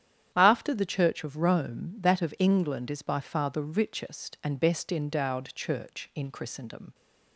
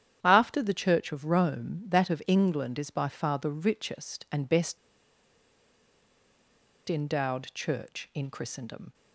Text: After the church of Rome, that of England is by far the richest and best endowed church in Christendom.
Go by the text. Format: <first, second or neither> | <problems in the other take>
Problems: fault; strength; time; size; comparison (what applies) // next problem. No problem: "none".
first | starts louder than the rest; strong; until 1.2 s; 10 dB; strong in the first // pauses between "best" and "endowed"; strong; at 4.7 s; 2.0 s long